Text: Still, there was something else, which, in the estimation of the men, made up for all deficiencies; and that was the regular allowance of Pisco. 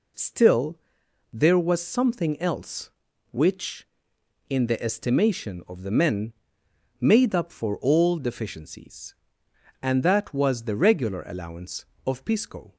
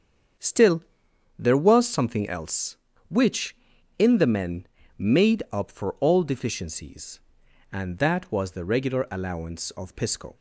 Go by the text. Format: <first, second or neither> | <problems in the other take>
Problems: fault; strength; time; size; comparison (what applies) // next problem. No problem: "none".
first | starts louder than the rest; strong; until 1.9 s; 7 dB // skips "the estimation of"; at 4.1 s